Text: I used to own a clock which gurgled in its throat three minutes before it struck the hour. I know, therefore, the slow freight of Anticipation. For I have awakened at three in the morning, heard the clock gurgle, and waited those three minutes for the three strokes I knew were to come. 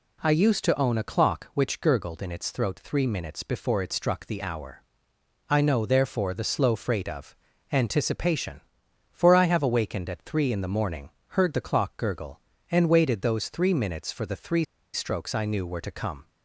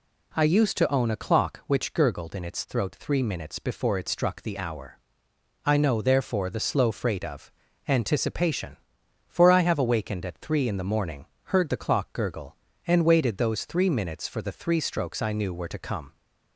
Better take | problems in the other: second | pauses between "of" and "Anticipation"; slight; at 7.3 s; 0.34 s long; slight in the second // pauses between "three" and "strokes"; slight; at 14.6 s; 0.28 s long

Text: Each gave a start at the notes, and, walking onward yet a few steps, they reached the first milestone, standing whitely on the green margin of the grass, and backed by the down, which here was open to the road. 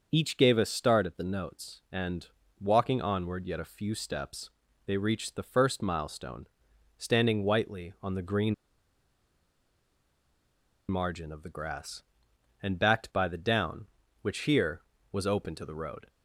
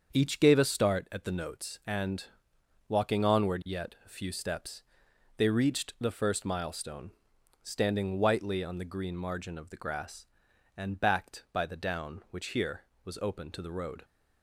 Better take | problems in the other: second | starts louder than the rest; until 1.1 s; 6 dB; also in the second // pauses between "green" and "margin"; strong; at 8.5 s; 2.3 s long

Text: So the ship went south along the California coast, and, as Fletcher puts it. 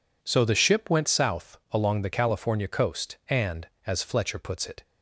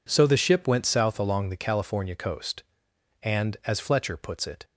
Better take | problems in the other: neither | none

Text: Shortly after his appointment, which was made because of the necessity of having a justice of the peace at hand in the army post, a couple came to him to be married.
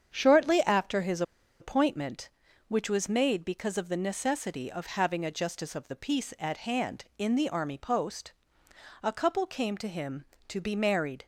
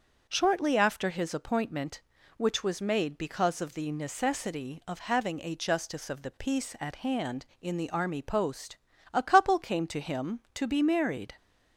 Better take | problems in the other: second | starts louder than the rest; strong; until 1.1 s; 8 dB; also in the second // pauses between "his" and "appointment"; at 1.2 s; 0.37 s long

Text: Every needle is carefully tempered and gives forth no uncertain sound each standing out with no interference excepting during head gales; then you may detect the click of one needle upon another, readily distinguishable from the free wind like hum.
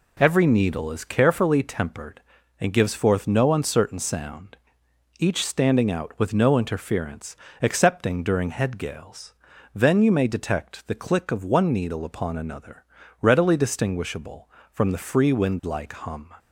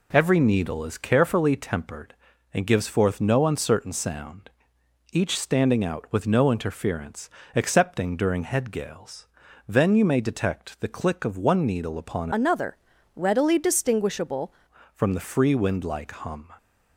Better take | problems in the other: first | pauses between "sound" and "each"; noticeable; at 4.4 s; 0.64 s long; noticeable in the first // pauses between "interference" and "excepting"; slight; at 7.2 s; 0.24 s long; slight in the first // changes voice from "another" to "distinguishable"; from 12.3 to 14.5 s; 2.2 s long

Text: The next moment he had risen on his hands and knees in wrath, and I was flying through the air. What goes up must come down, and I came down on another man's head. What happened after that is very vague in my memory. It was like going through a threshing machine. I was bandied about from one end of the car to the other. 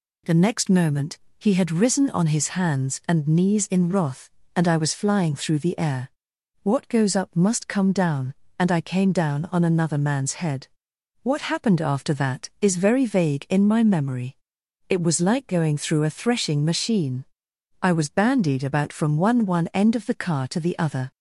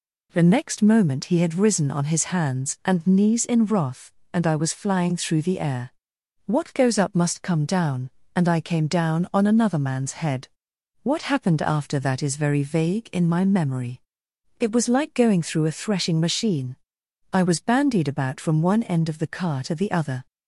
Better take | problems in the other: second | pauses between "moment" and "he"; slight; at 1.1 s; 0.20 s long // says "one" twice; at 19.4 s

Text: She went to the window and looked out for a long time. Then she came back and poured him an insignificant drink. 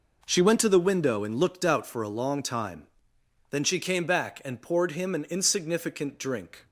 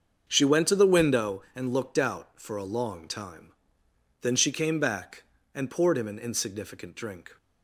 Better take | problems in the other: first | starts louder than the rest; until 1.4 s; 6.5 dB

